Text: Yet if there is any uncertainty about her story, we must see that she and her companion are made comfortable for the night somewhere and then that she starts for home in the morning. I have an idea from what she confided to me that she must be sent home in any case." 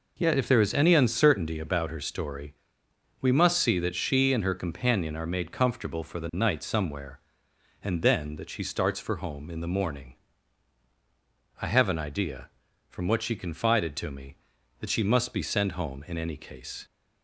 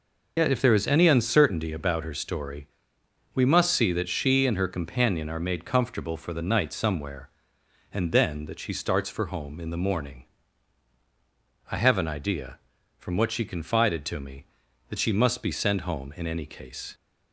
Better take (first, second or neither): first